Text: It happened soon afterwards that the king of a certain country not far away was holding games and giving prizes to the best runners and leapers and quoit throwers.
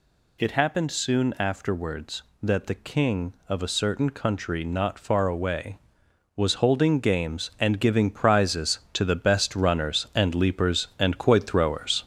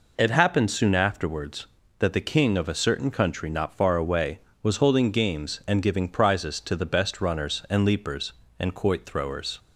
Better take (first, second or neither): second